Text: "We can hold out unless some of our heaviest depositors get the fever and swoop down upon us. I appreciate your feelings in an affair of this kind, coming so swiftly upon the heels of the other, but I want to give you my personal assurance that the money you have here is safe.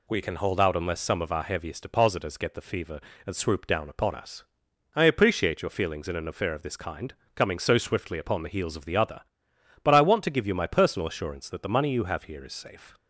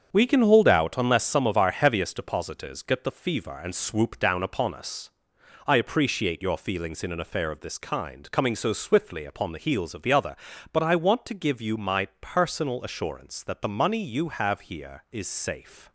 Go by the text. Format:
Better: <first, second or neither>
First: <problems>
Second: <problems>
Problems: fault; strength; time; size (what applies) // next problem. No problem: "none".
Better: first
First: none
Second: gets quieter; strong; throughout; 7.5 dB